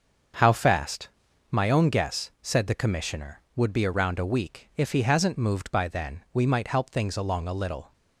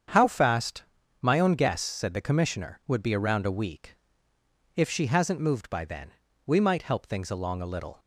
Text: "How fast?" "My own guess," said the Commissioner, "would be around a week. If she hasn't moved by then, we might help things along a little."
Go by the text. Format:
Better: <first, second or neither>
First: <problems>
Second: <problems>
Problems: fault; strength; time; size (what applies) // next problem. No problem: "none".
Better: second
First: starts louder than the rest; until 1.8 s; 7 dB // says "he" for "she"; at 4.9 s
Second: starts louder than the rest; strong; until 1.4 s; 8 dB